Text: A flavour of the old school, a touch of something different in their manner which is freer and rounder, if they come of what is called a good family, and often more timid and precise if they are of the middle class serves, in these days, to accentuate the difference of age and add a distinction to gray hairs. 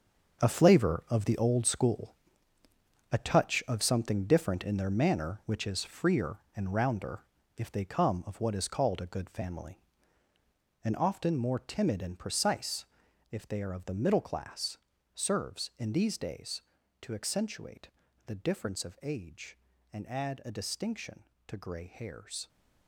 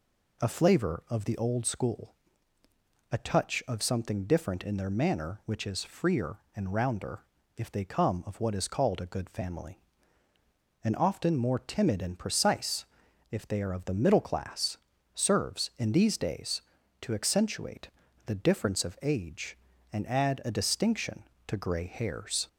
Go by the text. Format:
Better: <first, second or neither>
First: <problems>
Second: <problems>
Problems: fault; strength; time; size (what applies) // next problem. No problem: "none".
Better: second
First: gets quieter; strong; throughout; 10.5 dB // pauses between "precise" and "if"; at 12.8 s; 0.44 s long // pauses between "class" and "serves"; slight; at 14.7 s; 0.36 s long // pauses between "accentuate" and "the"; slight; at 17.8 s; 0.36 s long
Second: pauses between "precise" and "if"; at 12.8 s; 0.44 s long // pauses between "class" and "serves"; slight; at 14.7 s; 0.36 s long // pauses between "accentuate" and "the"; slight; at 17.8 s; 0.36 s long